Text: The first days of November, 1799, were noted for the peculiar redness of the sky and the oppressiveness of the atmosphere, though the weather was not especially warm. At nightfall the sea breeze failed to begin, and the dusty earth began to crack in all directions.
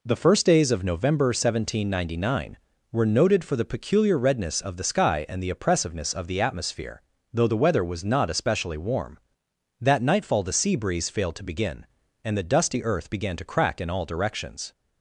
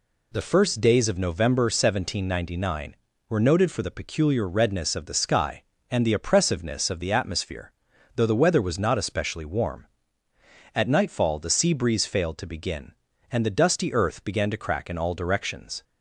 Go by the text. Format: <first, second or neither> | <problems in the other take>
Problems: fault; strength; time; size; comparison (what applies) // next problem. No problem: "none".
second | says "That" for "At"; at 9.7 s